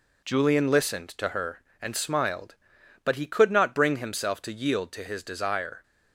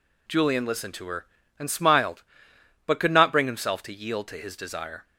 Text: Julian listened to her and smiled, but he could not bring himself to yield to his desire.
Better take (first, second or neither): first